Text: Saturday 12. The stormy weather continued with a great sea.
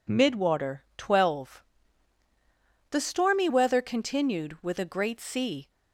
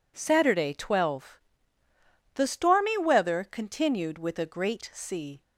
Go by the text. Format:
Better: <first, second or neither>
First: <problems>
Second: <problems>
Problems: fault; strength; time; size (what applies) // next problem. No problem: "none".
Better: second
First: says "Midwater" for "Saturday"; at 0.0 s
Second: none